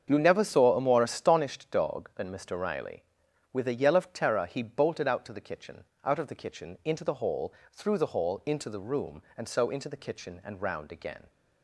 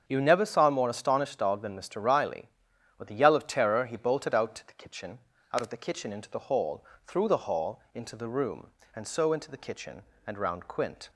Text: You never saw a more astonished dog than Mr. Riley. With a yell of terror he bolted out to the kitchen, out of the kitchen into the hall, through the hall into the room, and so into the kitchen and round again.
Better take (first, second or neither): first